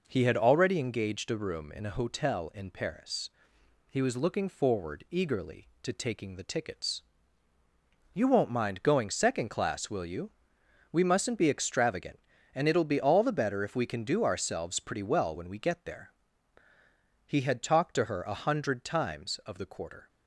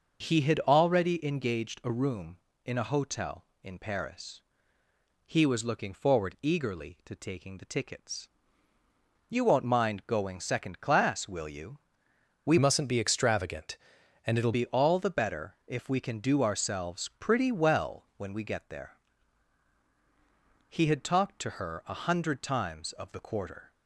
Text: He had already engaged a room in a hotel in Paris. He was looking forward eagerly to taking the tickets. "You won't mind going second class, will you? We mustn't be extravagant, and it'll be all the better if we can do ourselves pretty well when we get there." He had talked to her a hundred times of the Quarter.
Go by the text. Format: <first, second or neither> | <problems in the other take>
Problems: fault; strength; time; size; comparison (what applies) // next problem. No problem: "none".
first | changes voice from "mustn't" to "it'll"; from 12.5 to 14.5 s; 2.0 s long